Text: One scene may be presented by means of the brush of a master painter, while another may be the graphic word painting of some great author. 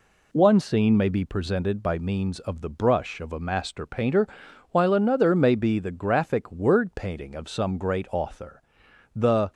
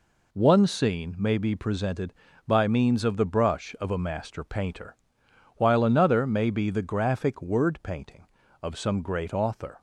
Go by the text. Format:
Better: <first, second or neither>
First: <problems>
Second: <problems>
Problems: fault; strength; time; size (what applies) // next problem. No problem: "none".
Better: second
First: goes on to say "The"; slight; from 9.1 s on; 0.38 s long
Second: none